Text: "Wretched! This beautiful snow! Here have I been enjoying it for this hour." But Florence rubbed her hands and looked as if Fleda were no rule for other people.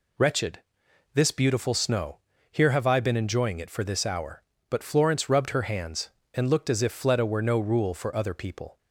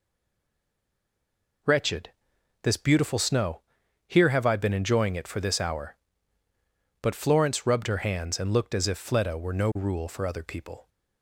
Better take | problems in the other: first | stays silent before the first word; noticeable; until 1.6 s; 1.6 s long

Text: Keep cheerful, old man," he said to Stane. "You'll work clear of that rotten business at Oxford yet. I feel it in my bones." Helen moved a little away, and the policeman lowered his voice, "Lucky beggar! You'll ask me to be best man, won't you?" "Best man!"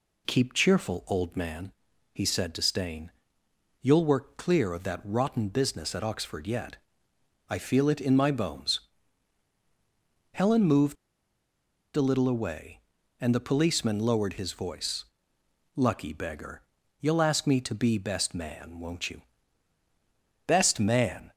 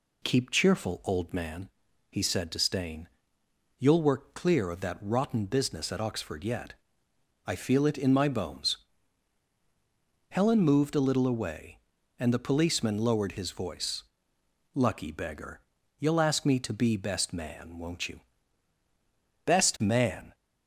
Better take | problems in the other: second | pauses between "moved" and "a"; at 10.9 s; 1.0 s long

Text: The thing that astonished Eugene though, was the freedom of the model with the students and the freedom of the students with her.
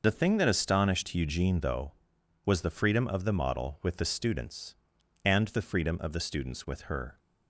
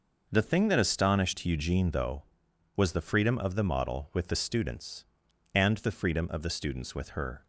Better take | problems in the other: second | loses the start of "The"; at 0.0 s; 55 ms

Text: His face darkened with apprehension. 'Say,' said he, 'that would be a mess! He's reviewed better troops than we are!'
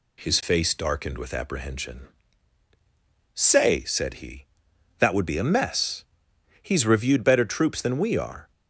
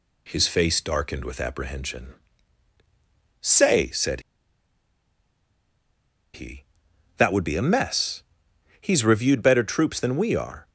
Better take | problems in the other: first | pauses between "said" and "he"; strong; at 4.2 s; 2.1 s long

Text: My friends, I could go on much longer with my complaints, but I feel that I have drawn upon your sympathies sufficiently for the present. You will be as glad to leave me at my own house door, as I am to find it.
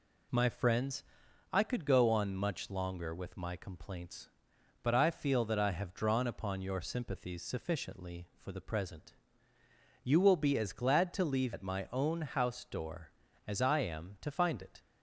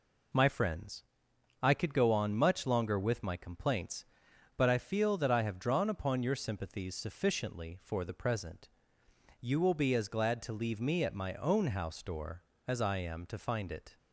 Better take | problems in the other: second | skips "me"; at 11.5 s

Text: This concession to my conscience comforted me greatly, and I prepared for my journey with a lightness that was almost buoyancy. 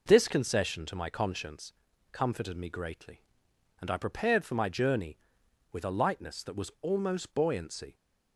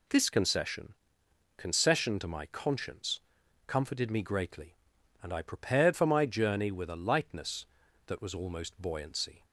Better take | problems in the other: first | says "concession" twice; at 1.5 s // pauses between "conscience" and "comforted"; noticeable; at 3.2 s; 0.46 s long; also in the first

